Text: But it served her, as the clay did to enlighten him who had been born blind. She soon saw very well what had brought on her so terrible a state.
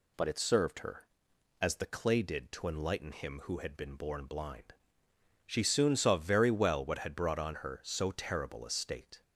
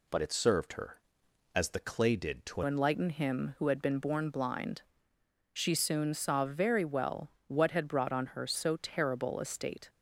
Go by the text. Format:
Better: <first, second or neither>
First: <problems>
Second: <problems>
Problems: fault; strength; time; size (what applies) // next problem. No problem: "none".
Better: first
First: none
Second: changes voice at "enlighten"; from 2.6 s on; 7.2 s long // pauses between "well" and "what"; slight; at 7.2 s; 0.18 s long